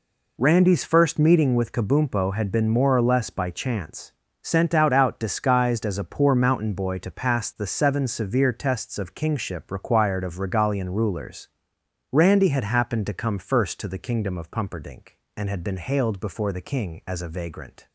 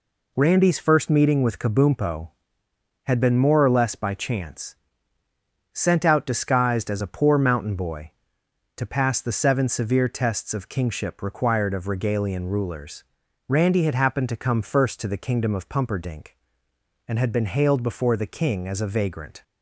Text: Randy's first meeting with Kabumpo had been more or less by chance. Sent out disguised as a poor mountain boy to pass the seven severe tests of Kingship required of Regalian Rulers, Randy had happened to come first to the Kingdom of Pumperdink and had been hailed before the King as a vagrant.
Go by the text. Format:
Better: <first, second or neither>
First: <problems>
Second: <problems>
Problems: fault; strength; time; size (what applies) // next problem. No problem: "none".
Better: second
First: says "out" twice; at 4.9 s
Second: none